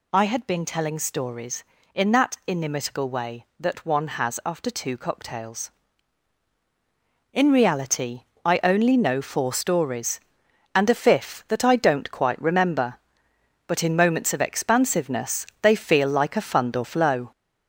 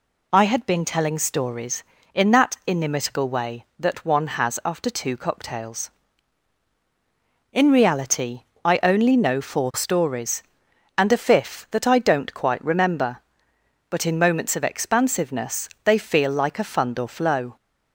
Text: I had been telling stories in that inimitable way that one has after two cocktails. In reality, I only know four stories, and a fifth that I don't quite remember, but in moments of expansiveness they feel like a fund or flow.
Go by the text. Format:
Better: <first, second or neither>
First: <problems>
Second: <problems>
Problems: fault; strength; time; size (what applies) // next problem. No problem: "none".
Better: second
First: gets louder; noticeable; throughout; 4.5 dB // pauses between "expansiveness" and "they"; slight; at 15.4 s; 0.16 s long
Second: pauses between "expansiveness" and "they"; slight; at 15.6 s; 0.16 s long